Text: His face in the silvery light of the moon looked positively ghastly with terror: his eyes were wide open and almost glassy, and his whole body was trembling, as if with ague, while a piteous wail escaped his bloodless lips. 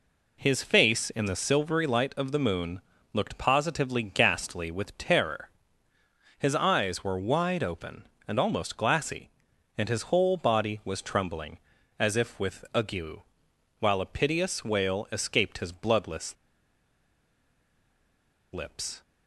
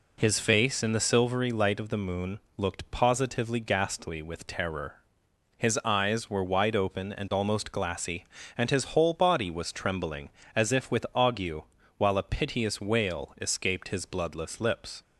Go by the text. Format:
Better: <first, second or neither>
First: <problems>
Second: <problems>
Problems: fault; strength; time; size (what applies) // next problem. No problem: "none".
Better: second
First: pauses between "moon" and "looked"; slight; at 2.7 s; 0.34 s long // pauses between "bloodless" and "lips"; strong; at 16.3 s; 2.1 s long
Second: pauses between "moon" and "looked"; slight; at 2.4 s; 0.16 s long